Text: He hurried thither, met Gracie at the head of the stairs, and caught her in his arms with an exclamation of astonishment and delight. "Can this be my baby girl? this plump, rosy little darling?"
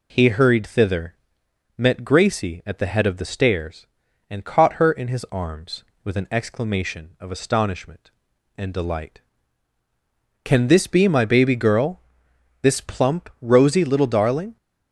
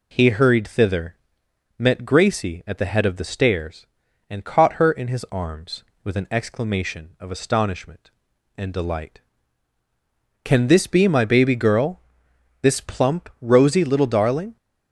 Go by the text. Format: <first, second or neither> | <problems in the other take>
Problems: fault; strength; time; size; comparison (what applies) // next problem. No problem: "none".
neither | none